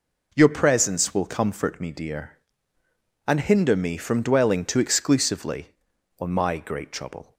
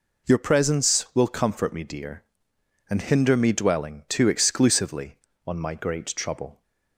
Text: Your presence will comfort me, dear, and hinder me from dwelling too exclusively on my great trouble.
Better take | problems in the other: first | skips "from"; at 3.5 s

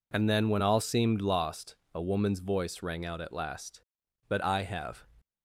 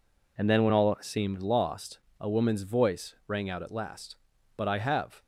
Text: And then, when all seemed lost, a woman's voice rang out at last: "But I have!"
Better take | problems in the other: neither | none

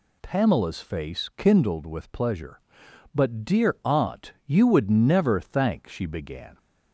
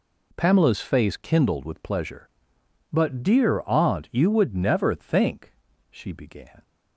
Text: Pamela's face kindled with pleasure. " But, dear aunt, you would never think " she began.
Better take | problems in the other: second | says "thank" for "think"; at 5.3 s

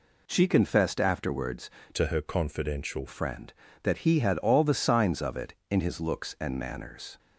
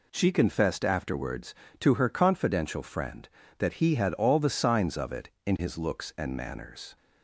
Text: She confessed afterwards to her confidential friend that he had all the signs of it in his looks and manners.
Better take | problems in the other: second | changes voice from "to" to "confidential"; from 1.9 to 3.0 s; 1.1 s long

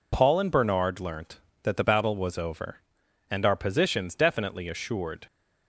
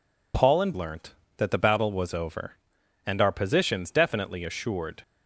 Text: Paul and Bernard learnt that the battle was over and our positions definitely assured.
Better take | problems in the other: first | skips "Bernard"; at 0.7 s

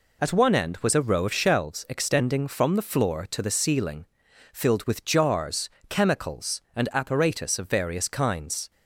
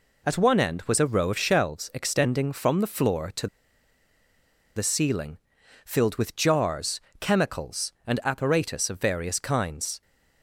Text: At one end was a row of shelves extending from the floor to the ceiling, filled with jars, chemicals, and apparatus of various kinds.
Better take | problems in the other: first | pauses between "to" and "the"; strong; at 3.4 s; 1.3 s long

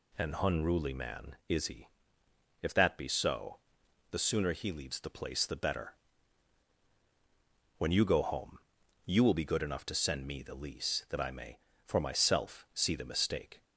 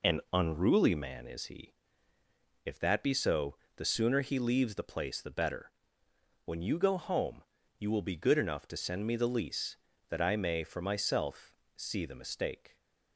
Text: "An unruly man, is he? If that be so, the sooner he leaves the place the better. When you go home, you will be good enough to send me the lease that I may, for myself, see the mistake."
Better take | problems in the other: neither | none

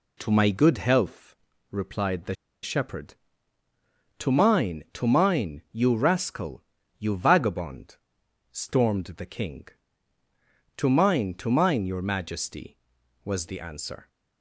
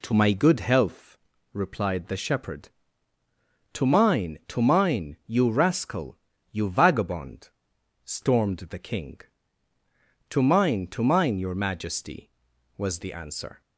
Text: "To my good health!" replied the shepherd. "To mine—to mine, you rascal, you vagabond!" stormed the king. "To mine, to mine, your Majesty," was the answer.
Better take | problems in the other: second | pauses between "the" and "shepherd"; slight; at 2.3 s; 0.28 s long

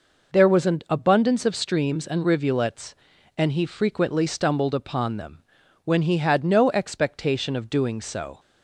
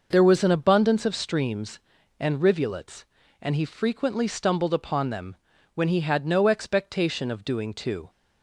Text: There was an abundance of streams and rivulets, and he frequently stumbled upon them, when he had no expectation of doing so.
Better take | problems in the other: first | says "too" for "so"; at 7.7 s

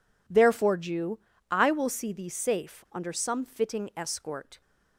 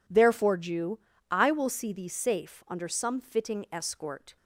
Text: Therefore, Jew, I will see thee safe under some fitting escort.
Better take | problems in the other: neither | none

